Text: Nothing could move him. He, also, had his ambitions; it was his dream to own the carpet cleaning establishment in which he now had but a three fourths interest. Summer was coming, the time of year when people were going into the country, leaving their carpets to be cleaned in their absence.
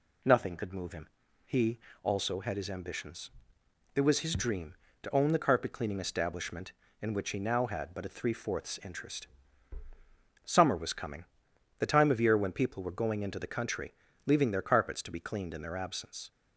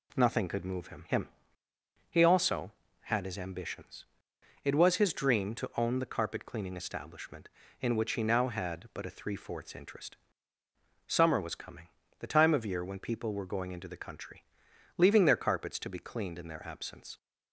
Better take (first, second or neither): first